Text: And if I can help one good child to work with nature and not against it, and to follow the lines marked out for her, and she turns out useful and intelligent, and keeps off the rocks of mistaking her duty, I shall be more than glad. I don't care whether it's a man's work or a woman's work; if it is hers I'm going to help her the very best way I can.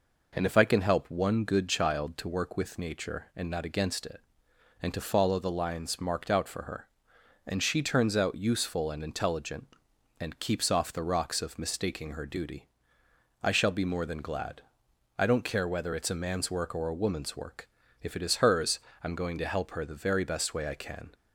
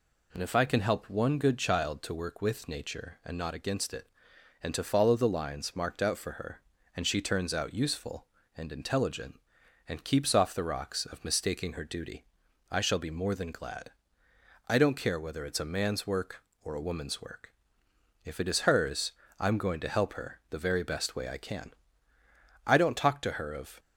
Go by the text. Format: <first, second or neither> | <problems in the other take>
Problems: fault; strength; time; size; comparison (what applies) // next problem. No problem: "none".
first | pauses between "hers" and "I'm"; slight; at 19.1 s; 0.26 s long; slight in the first // goes on to say "I don't talk to her of"; noticeable; from 22.6 s on; 1.1 s long